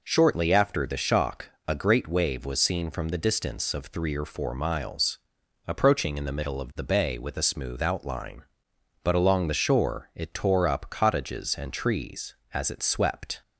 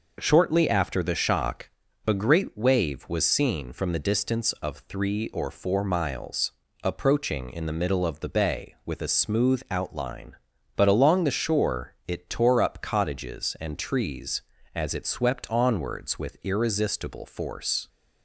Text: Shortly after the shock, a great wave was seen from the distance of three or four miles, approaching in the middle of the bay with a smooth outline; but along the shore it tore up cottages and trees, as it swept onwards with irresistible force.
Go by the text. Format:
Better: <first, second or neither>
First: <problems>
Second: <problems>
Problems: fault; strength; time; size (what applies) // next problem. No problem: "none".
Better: second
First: stops before "onwards with irresistible force"; at 13.4 s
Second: none